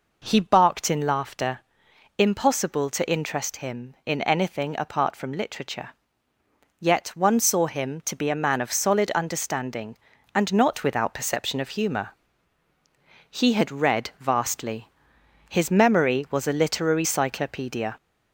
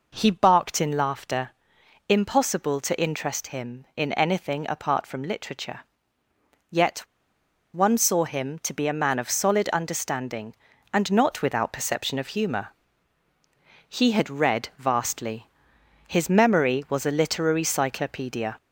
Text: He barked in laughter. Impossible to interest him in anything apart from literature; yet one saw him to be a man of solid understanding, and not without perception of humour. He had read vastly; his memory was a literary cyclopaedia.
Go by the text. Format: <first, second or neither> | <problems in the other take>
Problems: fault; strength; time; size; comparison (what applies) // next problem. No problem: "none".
first | pauses between "yet" and "one"; noticeable; at 6.9 s; 0.74 s long